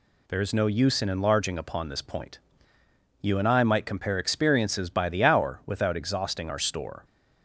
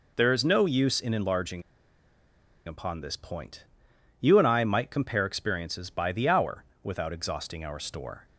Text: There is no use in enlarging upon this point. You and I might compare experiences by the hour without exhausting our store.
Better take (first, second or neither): first